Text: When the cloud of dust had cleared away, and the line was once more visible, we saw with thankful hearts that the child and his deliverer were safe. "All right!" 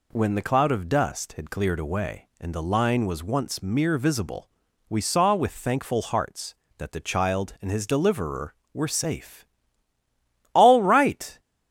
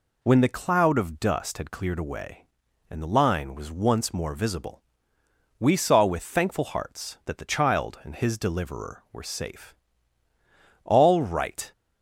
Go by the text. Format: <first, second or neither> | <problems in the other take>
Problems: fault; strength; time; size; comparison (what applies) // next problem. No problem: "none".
second | says "mere" for "more"; at 3.6 s